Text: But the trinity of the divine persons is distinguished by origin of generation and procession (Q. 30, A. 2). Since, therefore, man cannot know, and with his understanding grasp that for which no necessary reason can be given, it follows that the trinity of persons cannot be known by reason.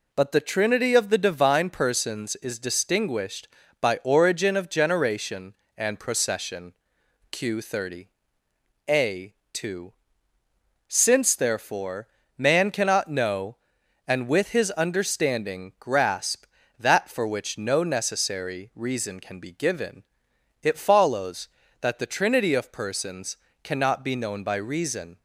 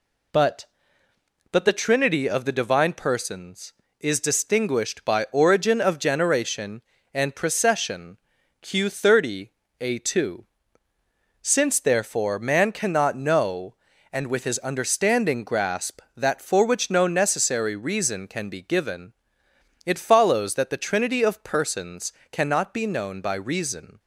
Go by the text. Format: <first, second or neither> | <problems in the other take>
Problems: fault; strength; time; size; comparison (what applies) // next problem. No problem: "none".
first | says "But" twice; at 1.5 s // pauses between "persons" and "cannot"; slight; at 22.1 s; 0.19 s long; slight in the first